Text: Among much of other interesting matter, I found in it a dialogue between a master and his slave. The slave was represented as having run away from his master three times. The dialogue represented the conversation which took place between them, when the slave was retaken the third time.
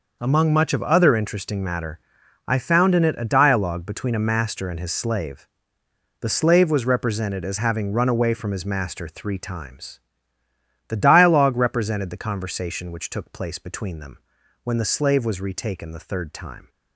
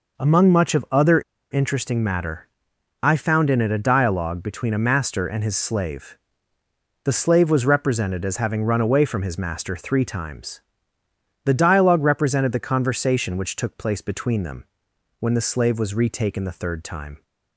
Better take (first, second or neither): first